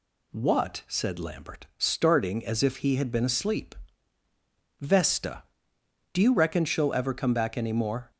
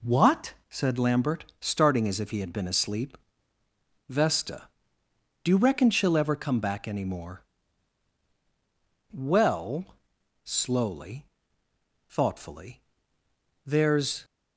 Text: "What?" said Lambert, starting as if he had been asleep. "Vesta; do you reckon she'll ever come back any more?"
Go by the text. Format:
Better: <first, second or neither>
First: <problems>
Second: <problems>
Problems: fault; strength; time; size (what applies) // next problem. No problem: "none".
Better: first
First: none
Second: goes on to say "Well slowly thoughtfully there's"; strong; from 9.1 s on; 5.1 s long